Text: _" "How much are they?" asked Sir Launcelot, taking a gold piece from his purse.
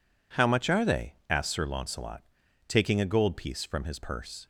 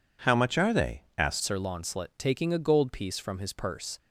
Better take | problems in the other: first | changes voice at "Sir"; from 1.4 s on; 2.5 s long

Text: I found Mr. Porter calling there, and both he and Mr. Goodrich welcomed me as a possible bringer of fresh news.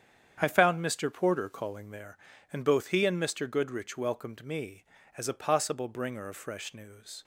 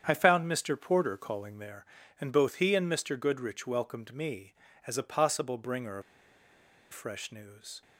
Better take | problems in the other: first | starts louder than the rest; strong; until 1.0 s; 8.5 dB; strong in the first // pauses between "of" and "fresh"; noticeable; at 6.0 s; 0.90 s long

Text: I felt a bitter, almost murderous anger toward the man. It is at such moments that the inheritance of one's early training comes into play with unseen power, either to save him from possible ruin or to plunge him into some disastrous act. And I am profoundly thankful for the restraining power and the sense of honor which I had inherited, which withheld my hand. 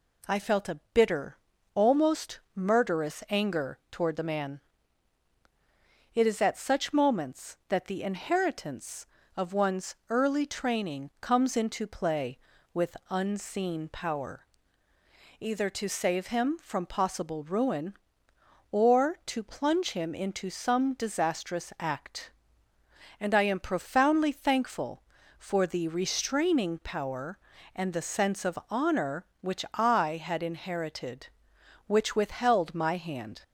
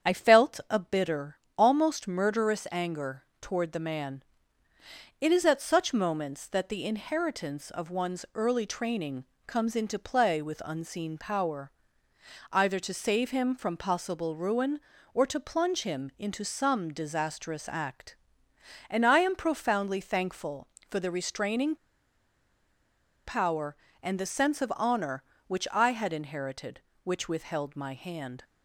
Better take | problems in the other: first | starts louder than the rest; strong; until 1.1 s; 8 dB // pauses between "anger" and "toward"; slight; at 3.2 s; 0.18 s long // pauses between "training" and "comes"; slight; at 9.2 s; 0.24 s long // pauses between "restraining" and "power"; strong; at 21.7 s; 1.4 s long

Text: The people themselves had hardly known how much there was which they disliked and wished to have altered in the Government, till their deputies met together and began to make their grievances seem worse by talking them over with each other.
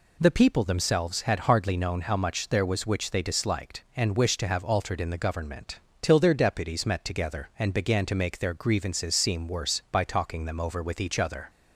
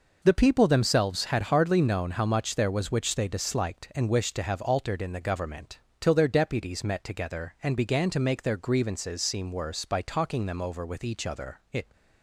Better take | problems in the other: first | goes on to say "It"; slight; from 11.7 s on; 0.20 s long

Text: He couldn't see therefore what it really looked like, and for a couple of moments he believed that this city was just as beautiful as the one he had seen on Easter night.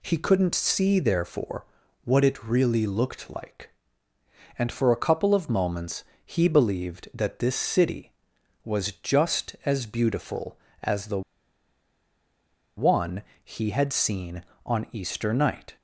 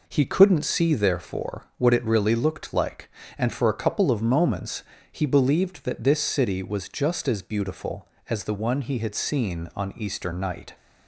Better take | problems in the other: second | pauses between "therefore" and "what"; at 1.6 s; 0.40 s long // pauses between "moments" and "he"; slight; at 6.0 s; 0.24 s long; slight in the second // pauses between "the" and "one"; strong; at 11.2 s; 1.5 s long // pauses between "one" and "he"; slight; at 13.2 s; 0.20 s long

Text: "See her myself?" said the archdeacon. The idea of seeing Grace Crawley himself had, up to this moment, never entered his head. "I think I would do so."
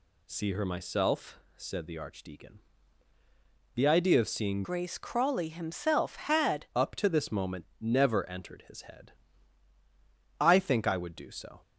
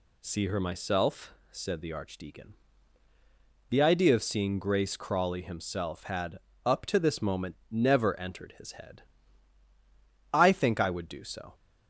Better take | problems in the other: second | changes voice from "Grace" to "had"; from 4.6 to 6.6 s; 2.0 s long

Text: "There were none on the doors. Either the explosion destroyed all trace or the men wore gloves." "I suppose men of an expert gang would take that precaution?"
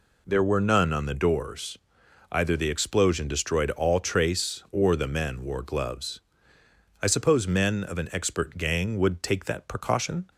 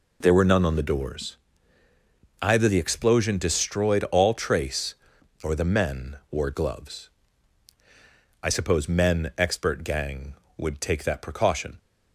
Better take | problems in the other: first | skips "of an"; at 9.3 s

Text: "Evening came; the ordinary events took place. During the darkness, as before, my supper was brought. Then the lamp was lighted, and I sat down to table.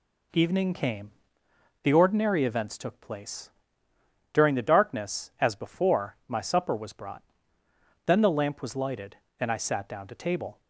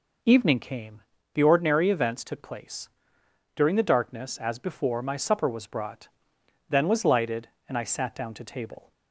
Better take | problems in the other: first | skips "the lamp"; at 6.8 s

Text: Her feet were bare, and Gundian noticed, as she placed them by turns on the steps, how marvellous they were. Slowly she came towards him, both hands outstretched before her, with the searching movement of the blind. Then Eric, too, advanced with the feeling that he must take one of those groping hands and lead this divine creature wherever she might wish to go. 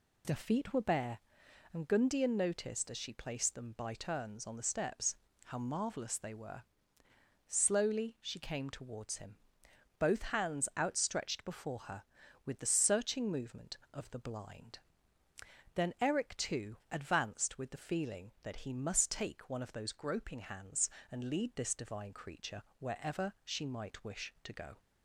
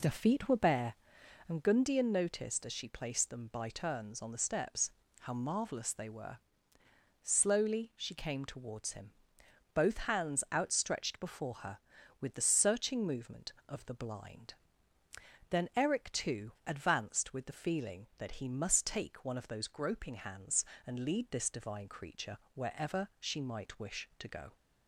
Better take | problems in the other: first | starts louder than the rest; slight; until 1.8 s; 3.5 dB // pauses between "creature" and "wherever"; slight; at 22.3 s; 0.18 s long; slight in the first

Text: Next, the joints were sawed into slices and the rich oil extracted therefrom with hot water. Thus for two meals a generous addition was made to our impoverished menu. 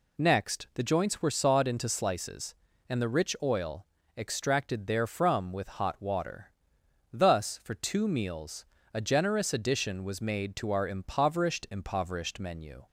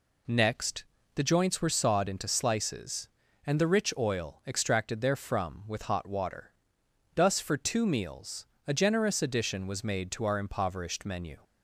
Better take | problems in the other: second | pauses between "oil" and "extracted"; slight; at 3.8 s; 0.30 s long // pauses between "meals" and "a"; slight; at 8.6 s; 0.30 s long; slight in the second // says "impoverished" twice; at 11.7 s

